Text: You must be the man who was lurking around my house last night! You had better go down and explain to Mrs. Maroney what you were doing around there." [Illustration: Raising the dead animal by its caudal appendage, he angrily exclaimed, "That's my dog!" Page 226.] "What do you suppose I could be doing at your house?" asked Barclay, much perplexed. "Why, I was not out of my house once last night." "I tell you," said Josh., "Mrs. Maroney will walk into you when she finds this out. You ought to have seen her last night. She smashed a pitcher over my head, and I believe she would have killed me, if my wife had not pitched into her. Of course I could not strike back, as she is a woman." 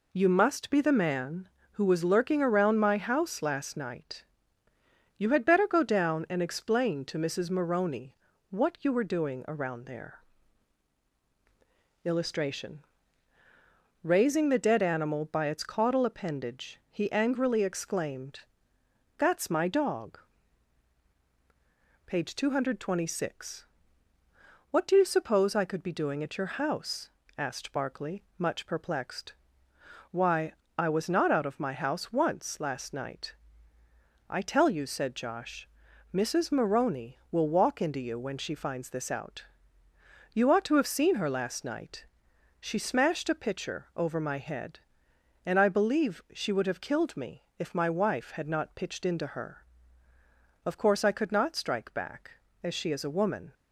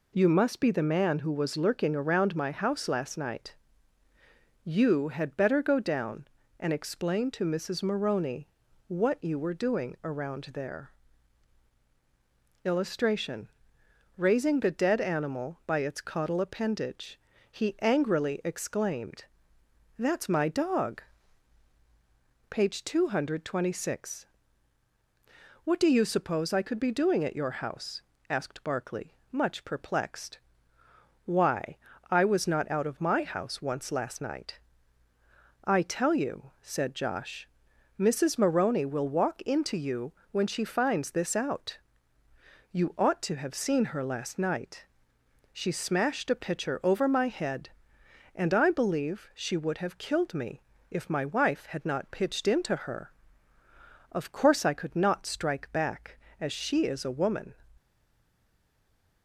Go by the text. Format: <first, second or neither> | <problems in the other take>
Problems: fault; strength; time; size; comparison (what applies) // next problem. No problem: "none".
first | pauses between "Maroney" and "what"; at 8.4 s; 0.40 s long; slight in the first // pauses between "you" and "when"; slight; at 40.1 s; 0.18 s long // stays silent after the last word; noticeable; from 57.7 s on; 1.5 s long